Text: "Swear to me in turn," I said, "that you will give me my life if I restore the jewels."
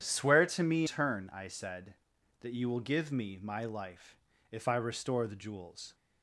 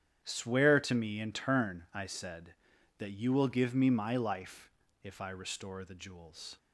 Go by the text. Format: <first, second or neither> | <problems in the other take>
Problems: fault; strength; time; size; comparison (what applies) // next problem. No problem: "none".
second | starts louder than the rest; strong; until 1.0 s; 9 dB; strong in the second // skips "in"; at 0.8 s // pauses between "life" and "if"; slight; at 4.1 s; 0.36 s long; slight in the second